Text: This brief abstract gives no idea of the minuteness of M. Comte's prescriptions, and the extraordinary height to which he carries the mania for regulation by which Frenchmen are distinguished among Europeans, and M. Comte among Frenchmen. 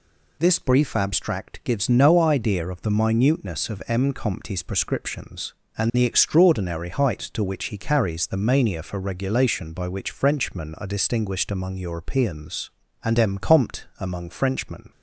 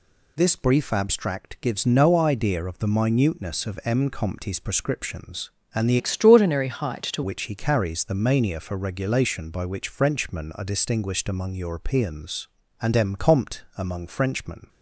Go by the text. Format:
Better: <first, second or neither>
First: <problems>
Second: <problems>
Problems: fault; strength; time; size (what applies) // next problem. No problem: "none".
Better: first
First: none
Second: changes voice from "extraordinary" to "to"; from 5.9 to 7.2 s; 1.3 s long